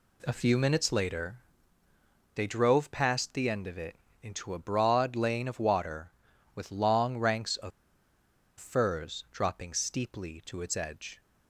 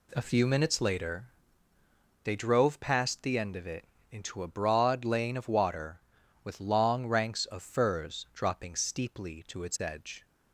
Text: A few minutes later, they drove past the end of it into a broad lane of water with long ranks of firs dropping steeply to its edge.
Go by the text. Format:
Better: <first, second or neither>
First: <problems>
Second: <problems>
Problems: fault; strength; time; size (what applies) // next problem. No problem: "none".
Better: second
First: pauses between "it" and "into"; slight; at 3.9 s; 0.26 s long // pauses between "of" and "firs"; noticeable; at 7.7 s; 0.89 s long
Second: pauses between "it" and "into"; slight; at 3.8 s; 0.26 s long